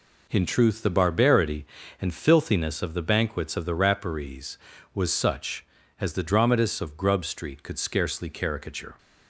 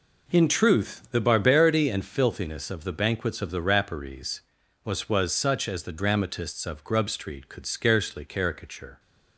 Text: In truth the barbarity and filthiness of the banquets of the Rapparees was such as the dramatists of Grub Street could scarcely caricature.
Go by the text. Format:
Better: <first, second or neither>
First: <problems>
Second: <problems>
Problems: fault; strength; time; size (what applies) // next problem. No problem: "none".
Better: first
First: none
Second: says "was" twice; at 5.0 s